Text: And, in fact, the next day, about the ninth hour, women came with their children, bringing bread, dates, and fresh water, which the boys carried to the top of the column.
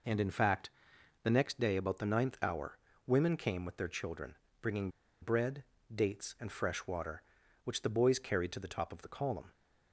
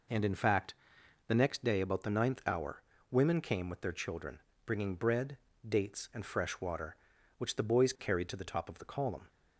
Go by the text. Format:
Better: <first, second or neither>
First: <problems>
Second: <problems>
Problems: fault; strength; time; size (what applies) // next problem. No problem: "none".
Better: second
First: pauses between "bringing" and "bread"; slight; at 4.9 s; 0.30 s long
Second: none